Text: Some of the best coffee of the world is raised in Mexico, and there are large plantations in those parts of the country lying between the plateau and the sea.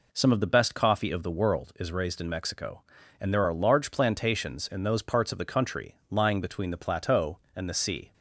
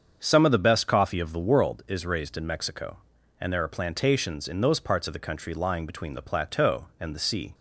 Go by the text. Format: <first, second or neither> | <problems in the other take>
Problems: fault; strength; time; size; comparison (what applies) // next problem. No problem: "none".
first | starts louder than the rest; until 1.2 s; 7 dB // skips "large"; at 3.6 s